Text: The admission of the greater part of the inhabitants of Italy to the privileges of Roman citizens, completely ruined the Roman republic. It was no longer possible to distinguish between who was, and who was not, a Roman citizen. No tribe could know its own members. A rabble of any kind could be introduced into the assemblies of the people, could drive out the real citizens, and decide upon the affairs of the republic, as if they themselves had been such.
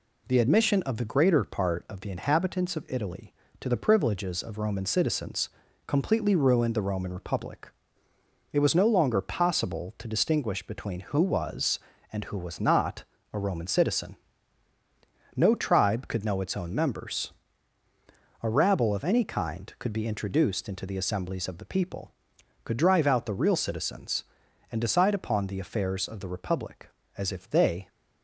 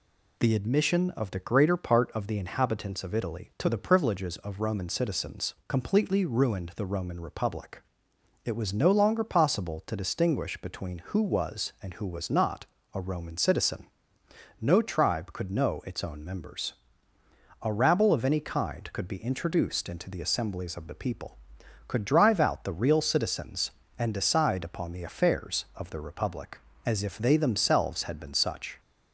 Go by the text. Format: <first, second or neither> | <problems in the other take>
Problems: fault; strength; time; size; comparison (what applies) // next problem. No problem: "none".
second | stops before "themselves had been such"; at 27.8 s